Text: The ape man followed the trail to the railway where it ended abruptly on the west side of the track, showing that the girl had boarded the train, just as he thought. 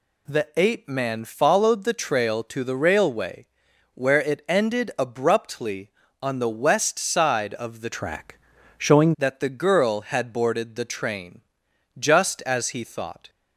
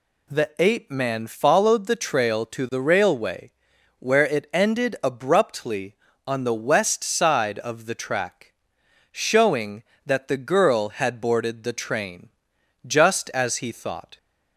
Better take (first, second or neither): second